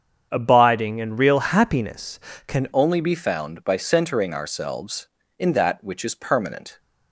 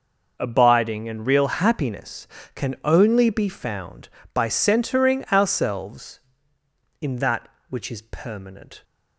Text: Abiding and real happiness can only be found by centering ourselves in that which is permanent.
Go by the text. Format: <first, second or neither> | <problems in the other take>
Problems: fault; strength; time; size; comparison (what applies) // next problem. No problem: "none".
second | starts louder than the rest; strong; until 1.3 s; 7.5 dB // changes voice at "only"; from 2.7 s on; 4.0 s long